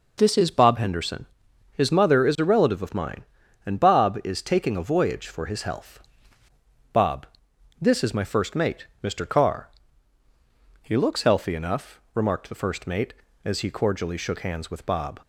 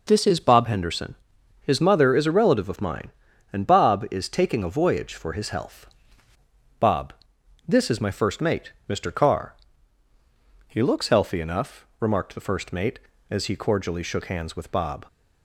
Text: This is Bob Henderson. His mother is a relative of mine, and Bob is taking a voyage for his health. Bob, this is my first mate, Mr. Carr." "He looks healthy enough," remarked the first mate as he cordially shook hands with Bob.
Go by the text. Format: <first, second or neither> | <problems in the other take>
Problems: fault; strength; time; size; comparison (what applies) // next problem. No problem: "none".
neither | none